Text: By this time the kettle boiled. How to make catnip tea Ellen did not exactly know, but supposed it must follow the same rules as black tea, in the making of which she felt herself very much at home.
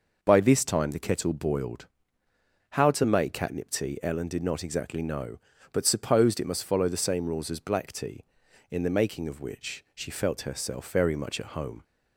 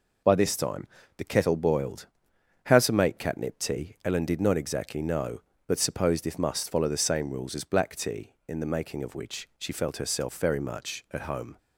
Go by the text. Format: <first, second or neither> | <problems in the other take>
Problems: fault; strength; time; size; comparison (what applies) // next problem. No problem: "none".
first | pauses between "time" and "the"; slight; at 0.8 s; 0.30 s long // says "if" for "it"; at 6.2 s